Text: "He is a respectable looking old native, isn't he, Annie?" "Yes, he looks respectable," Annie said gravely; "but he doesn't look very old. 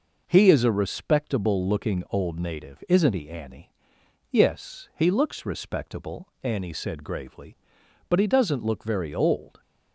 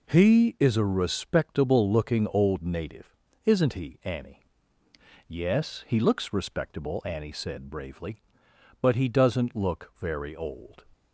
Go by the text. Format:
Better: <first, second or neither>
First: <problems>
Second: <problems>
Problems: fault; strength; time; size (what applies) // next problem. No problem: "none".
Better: first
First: none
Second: says "bravely" for "gravely"; at 7.7 s